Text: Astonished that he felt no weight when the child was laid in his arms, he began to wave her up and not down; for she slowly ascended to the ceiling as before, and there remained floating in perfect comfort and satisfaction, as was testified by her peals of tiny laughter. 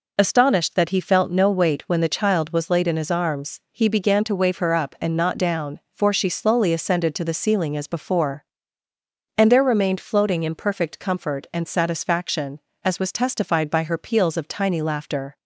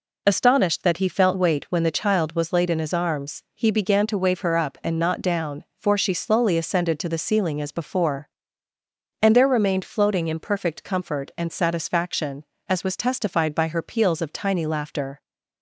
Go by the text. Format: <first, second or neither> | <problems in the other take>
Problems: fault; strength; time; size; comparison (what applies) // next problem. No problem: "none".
first | skips "no"; at 1.3 s